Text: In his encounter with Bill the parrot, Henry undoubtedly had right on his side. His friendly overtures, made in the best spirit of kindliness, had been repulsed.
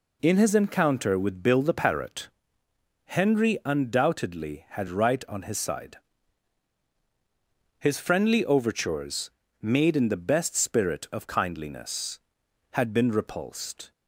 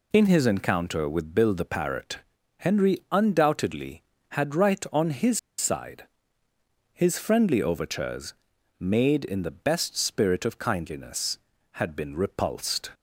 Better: first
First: none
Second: pauses between "his" and "side"; slight; at 5.3 s; 0.19 s long

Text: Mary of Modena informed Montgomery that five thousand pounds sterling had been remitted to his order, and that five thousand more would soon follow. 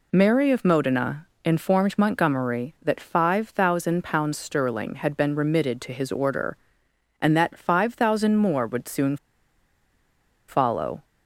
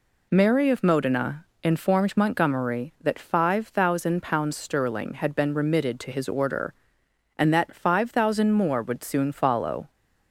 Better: second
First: pauses between "Modena" and "informed"; slight; at 1.2 s; 0.18 s long // pauses between "soon" and "follow"; strong; at 9.1 s; 1.3 s long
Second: pauses between "Modena" and "informed"; slight; at 1.4 s; 0.18 s long

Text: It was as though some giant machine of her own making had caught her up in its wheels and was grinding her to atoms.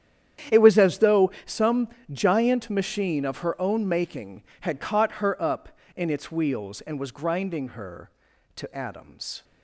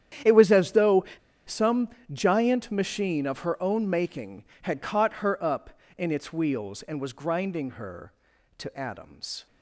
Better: first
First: starts louder than the rest; strong; until 1.6 s; 9.5 dB // pauses between "some" and "giant"; slight; at 1.8 s; 0.24 s long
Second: starts louder than the rest; strong; until 1.6 s; 9.5 dB // pauses between "though" and "some"; at 1.0 s; 0.41 s long // pauses between "some" and "giant"; slight; at 1.8 s; 0.24 s long

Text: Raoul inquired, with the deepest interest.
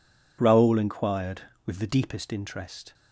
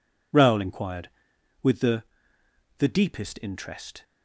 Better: first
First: none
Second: says "the" twice; at 2.7 s

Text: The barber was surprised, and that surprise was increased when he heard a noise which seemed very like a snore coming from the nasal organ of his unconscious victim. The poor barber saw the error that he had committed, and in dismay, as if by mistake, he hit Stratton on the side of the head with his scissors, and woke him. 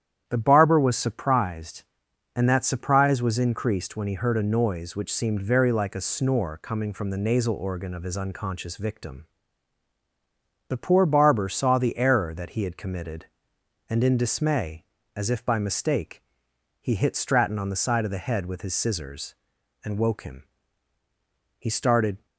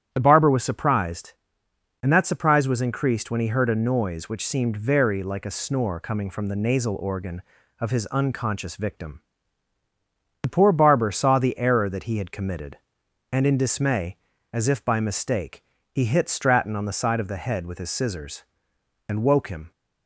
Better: second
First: starts louder than the rest; strong; until 1.2 s; 9.5 dB // goes on to say "He started"; noticeable; from 21.5 s on; 0.66 s long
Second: starts louder than the rest; strong; until 1.1 s; 10 dB

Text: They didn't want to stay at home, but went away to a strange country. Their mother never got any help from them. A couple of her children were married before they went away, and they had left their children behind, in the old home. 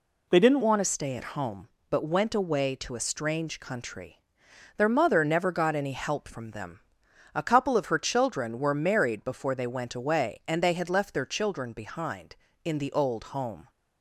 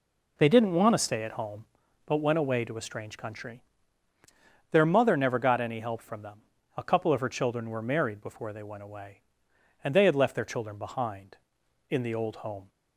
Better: second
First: changes voice at "want"; from 0.6 s on; 13.0 s long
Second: none

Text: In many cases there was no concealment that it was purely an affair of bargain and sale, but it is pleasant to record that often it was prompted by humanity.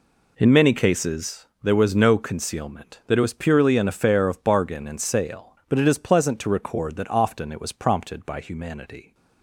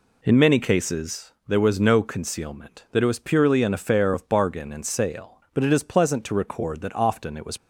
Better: first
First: pauses between "cases" and "there"; slight; at 1.4 s; 0.18 s long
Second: pauses between "cases" and "there"; slight; at 1.3 s; 0.16 s long // stops before "prompted by humanity"; at 7.5 s

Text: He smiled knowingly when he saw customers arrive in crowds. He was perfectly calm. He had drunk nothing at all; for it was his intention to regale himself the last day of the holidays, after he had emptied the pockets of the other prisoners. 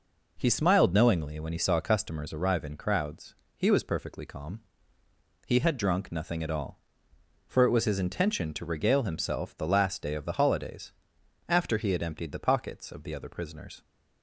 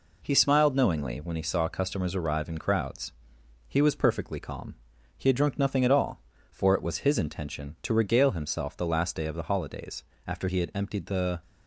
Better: first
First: none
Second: stops before "pockets of the other prisoners"; at 11.4 s

